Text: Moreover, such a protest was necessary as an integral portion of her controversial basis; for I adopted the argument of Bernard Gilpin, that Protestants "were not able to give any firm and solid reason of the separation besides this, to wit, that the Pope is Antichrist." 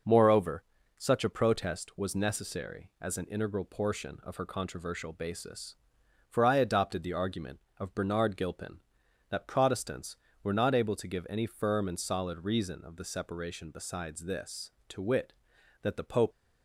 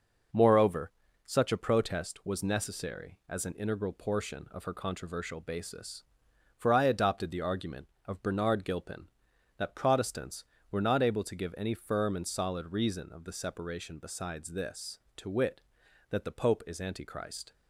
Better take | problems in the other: second | stops before "is Antichrist"; at 16.3 s

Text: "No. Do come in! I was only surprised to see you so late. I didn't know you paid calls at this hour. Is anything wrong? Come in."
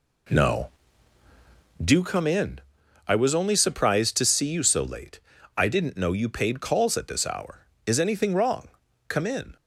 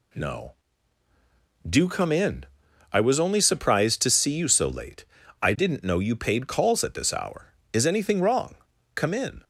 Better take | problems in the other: second | starts louder than the rest; slight; until 2.0 s; 3 dB

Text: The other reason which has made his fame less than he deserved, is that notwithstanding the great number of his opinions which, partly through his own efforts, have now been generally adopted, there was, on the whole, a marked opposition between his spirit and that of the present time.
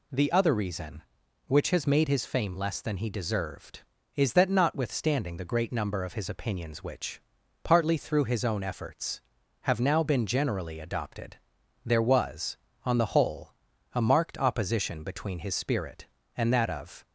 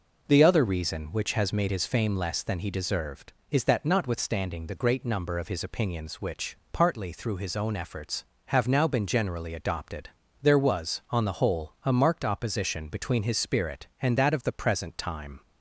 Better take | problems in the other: second | stops before "the present time"; at 17.0 s

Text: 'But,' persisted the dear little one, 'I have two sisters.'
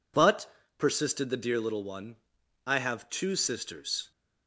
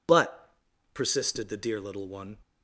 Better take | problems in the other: first | stops before "I have two sisters"; at 2.4 s

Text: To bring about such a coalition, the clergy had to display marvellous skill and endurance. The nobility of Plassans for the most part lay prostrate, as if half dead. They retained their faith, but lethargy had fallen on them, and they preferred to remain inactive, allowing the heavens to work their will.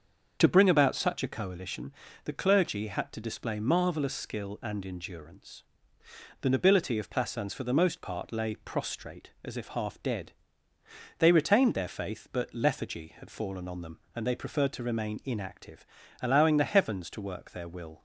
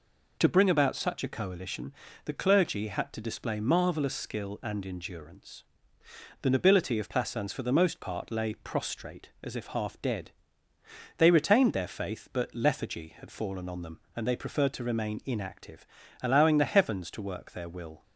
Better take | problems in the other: second | starts louder than the rest; until 1.4 s; 6.5 dB

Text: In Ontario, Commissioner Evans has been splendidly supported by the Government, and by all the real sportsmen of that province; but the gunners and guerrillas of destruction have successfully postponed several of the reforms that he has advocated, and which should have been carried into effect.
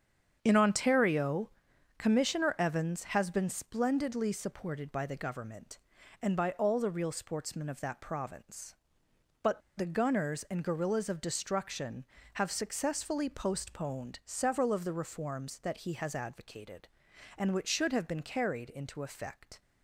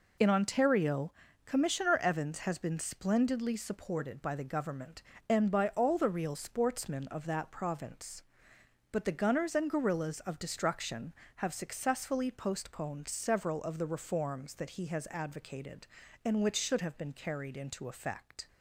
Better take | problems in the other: second | starts louder than the rest; strong; until 1.4 s; 7.5 dB // pauses between "but" and "the"; slight; at 9.5 s; 0.17 s long

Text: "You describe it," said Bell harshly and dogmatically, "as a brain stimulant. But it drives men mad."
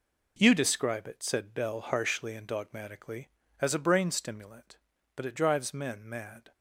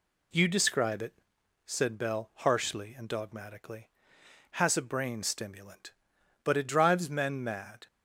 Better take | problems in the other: first | says "has" for "as"; at 4.5 s

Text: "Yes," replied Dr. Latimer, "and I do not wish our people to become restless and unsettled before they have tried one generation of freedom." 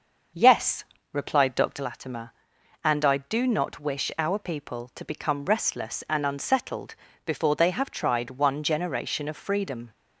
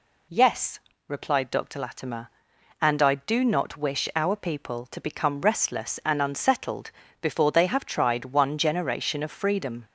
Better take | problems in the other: second | starts louder than the rest; until 2.0 s; 6.5 dB // pauses between "unsettled" and "before"; slight; at 6.9 s; 0.30 s long; slight in the second

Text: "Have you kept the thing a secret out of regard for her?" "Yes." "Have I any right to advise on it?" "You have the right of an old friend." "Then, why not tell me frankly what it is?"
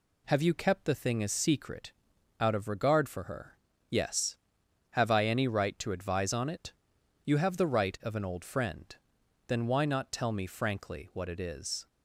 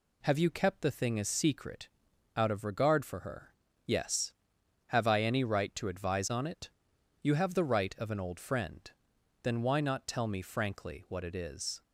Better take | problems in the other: neither | pauses between "secret" and "out"; noticeable; the same in both

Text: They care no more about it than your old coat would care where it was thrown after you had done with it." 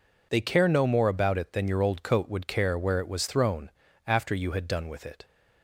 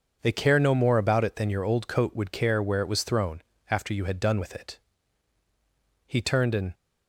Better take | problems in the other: first | pauses between "thrown" and "after"; slight; at 3.4 s; 0.30 s long; slight in the first // goes on to say "He turned and"; noticeable; from 6.0 s on; 0.66 s long

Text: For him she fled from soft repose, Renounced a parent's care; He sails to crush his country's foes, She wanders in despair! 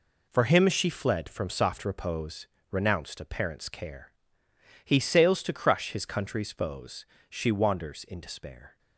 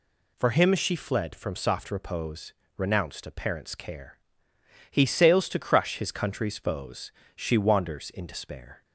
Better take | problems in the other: second | gets quieter; strong; throughout; 8 dB

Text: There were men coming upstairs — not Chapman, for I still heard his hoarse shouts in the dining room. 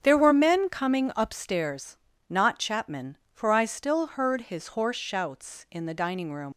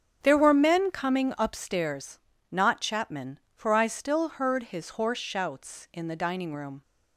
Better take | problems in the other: second | starts louder than the rest; strong; until 1.0 s; 8 dB; strong in the second // leaves "room" unfinished; at 6.5 s; 85 ms

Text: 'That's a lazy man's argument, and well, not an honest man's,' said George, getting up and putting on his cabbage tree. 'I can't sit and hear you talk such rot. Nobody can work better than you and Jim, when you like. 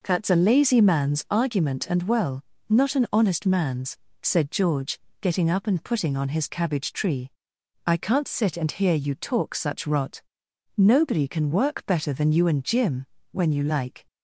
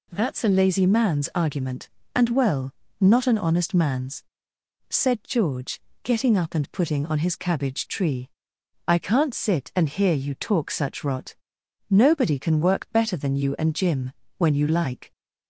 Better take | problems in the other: second | starts louder than the rest; noticeable; until 1.4 s; 5 dB

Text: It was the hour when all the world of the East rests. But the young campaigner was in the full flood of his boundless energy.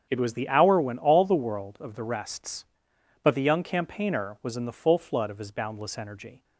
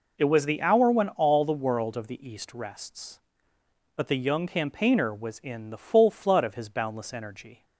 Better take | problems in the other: second | starts louder than the rest; strong; until 1.1 s; 7.5 dB // skips "East"; at 2.0 s

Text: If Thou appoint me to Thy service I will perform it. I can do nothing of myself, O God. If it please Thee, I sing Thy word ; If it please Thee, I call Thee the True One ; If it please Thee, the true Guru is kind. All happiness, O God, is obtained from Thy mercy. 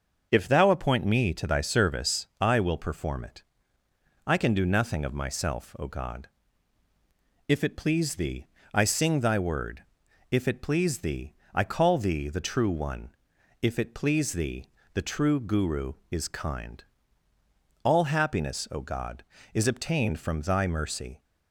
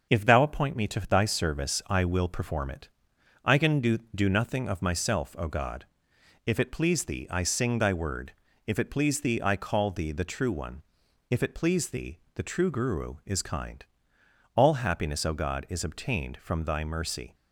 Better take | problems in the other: first | starts louder than the rest; noticeable; until 1.1 s; 6 dB; also in the first // says "do" twice; at 4.1 s

